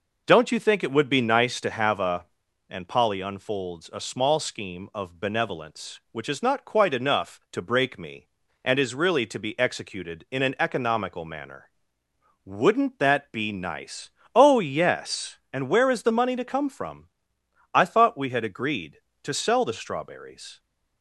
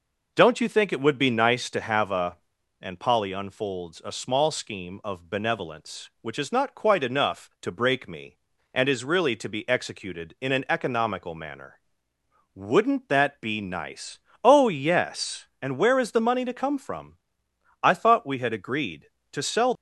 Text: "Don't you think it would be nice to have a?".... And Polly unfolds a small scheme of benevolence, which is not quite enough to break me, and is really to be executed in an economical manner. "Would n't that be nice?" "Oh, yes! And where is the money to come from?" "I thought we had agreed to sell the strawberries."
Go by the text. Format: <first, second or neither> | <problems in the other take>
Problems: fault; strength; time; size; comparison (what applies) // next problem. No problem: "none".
first | stops before "the strawberries"; at 19.7 s